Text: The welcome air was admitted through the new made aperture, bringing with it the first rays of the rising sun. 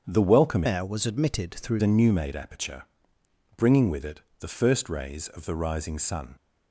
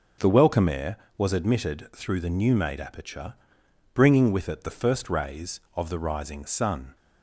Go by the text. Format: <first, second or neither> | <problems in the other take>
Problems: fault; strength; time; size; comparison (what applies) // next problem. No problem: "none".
second | starts louder than the rest; strong; until 1.0 s; 7.5 dB // changes voice from "air" to "through"; from 0.6 to 1.8 s; 1.2 s long // pauses between "it" and "the"; slight; at 4.1 s; 0.20 s long